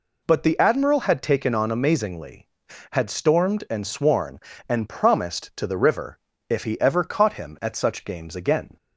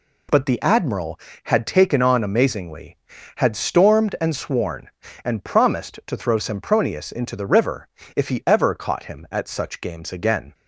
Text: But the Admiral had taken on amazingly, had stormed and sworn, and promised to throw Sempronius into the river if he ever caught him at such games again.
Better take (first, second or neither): second